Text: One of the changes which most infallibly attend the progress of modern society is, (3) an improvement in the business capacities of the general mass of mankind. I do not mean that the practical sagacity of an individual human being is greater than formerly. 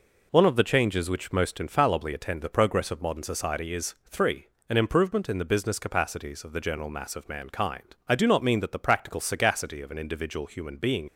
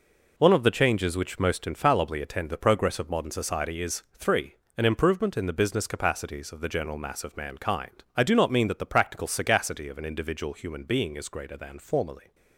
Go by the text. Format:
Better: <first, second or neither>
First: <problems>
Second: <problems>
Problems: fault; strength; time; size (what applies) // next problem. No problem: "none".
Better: second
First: stops before "is greater than formerly"; at 11.0 s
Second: none